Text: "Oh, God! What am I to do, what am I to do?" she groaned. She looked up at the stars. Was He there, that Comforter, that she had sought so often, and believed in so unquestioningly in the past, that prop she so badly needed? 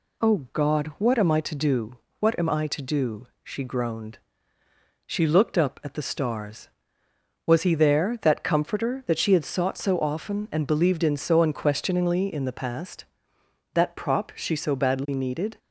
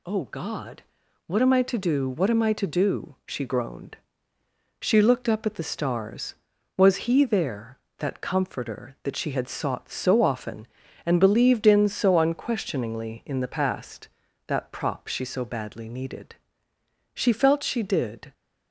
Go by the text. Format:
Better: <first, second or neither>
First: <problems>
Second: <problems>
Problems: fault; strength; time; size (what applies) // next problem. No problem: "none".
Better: first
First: none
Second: goes on to say "She felt she did"; noticeable; from 17.1 s on; 1.1 s long